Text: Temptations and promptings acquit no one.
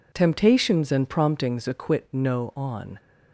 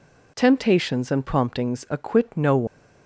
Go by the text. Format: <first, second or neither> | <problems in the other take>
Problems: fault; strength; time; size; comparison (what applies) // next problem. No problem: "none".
second | says "on" for "one"; at 2.5 s